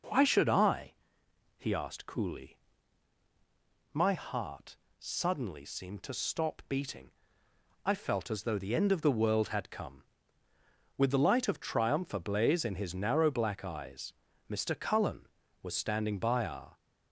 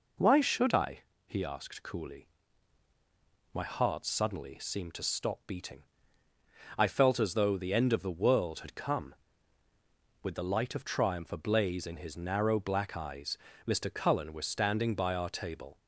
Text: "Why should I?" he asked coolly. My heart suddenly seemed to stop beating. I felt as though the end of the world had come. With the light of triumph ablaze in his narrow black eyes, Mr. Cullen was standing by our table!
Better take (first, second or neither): second